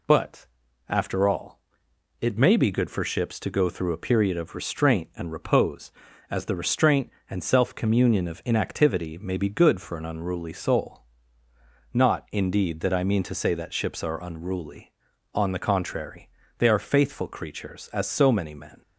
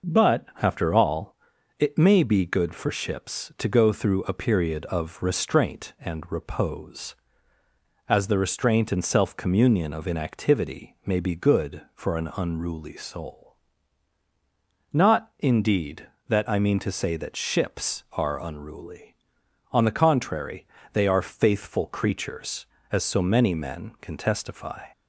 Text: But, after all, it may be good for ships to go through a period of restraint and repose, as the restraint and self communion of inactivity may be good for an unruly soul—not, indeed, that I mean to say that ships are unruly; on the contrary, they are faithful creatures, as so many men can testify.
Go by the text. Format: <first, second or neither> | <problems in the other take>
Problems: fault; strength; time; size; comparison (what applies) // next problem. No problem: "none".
second | stops before "can testify"; at 18.8 s